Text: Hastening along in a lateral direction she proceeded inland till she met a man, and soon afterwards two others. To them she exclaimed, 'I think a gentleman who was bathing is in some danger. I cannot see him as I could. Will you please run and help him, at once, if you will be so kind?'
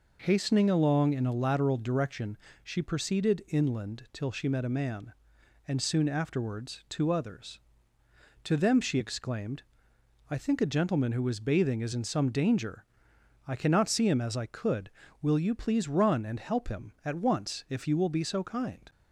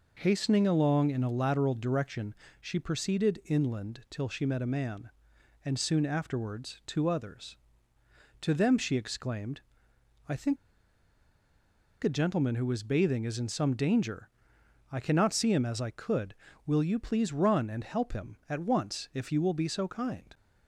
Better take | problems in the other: first | pauses between "direction" and "she"; slight; at 2.3 s; 0.26 s long; slight in the first // pauses between "think" and "a"; strong; at 10.5 s; 1.4 s long

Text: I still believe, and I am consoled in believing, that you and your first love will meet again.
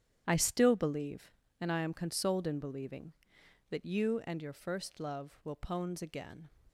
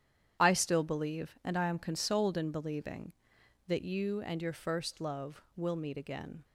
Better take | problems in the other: second | starts louder than the rest; strong; until 1.2 s; 10 dB; strong in the second // says "pones" for "meet"; at 5.5 s

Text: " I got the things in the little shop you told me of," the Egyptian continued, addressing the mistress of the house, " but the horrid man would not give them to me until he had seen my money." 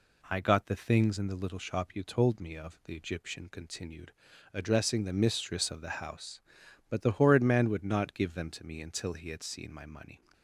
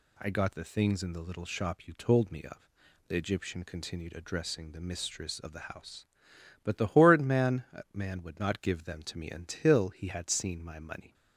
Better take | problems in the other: first | says "man" twice; at 7.9 s

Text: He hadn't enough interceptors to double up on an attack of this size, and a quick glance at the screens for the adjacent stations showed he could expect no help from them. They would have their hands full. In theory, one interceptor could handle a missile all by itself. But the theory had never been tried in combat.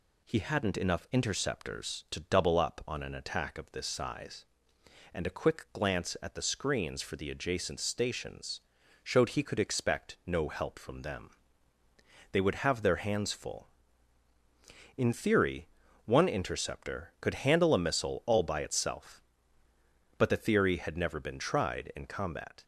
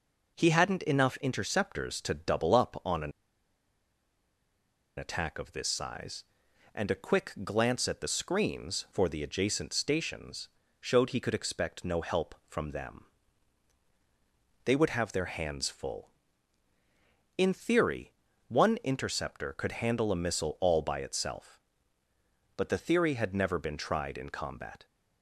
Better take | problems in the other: first | pauses between "an" and "attack"; strong; at 3.1 s; 1.8 s long // pauses between "stations" and "showed"; slight; at 10.4 s; 0.32 s long; also in the first

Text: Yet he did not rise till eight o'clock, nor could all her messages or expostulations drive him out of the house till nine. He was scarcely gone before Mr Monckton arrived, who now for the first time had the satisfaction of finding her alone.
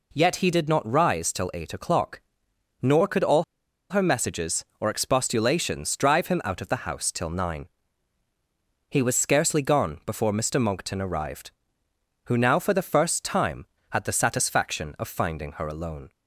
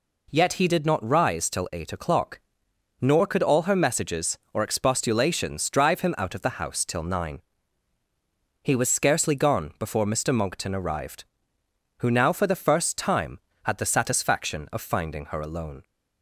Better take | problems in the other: second | pauses between "all" and "her"; noticeable; at 3.4 s; 0.46 s long

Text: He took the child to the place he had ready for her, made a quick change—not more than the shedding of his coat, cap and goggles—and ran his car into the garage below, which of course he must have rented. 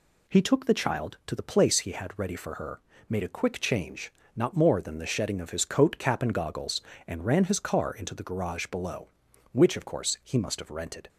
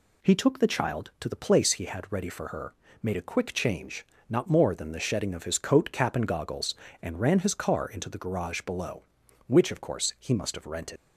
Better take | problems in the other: first | leaves "rented" unfinished; at 10.9 s; 80 ms

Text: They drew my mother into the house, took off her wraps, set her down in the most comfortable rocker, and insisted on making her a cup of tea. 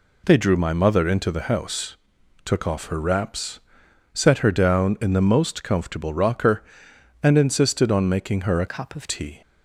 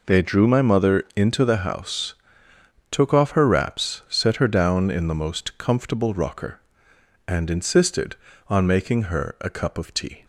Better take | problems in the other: second | changes voice from "cup" to "of"; from 8.6 to 9.0 s; 0.4 s long

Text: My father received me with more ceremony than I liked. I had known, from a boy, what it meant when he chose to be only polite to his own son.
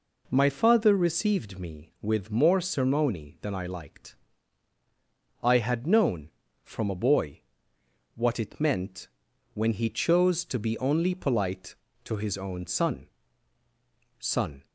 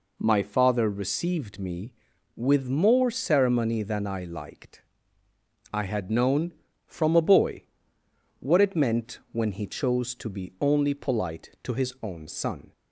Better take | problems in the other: second | pauses between "meant" and "when"; noticeable; at 9.0 s; 0.48 s long // says "son" twice; at 14.1 s

